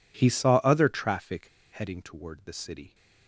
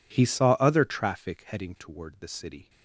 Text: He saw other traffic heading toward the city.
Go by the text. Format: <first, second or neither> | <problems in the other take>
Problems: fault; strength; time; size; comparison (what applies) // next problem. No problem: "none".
second | pauses between "traffic" and "heading"; slight; at 1.4 s; 0.27 s long